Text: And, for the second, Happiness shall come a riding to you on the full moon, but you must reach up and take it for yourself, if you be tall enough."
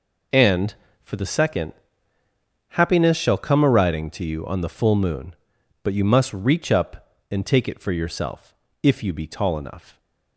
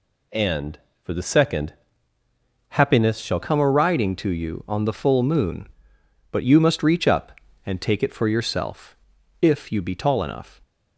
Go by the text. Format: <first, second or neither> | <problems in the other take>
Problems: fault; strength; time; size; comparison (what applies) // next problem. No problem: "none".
first | changes voice at "come"; from 3.3 s on; 7.2 s long